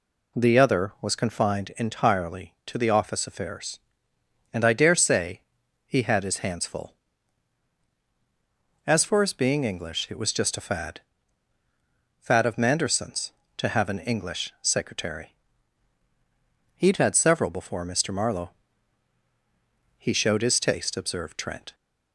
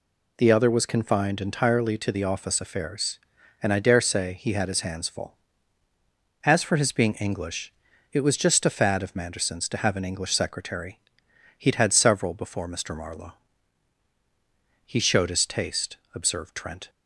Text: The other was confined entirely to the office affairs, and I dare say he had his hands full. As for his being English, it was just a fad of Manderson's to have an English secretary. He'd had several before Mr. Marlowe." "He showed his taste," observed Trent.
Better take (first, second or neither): second